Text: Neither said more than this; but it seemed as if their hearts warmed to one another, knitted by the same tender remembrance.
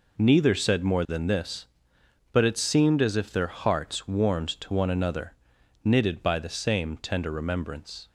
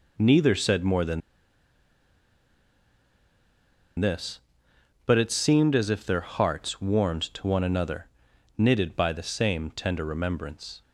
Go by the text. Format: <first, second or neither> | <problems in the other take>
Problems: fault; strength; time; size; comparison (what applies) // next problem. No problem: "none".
first | pauses between "than" and "this"; strong; at 1.2 s; 2.7 s long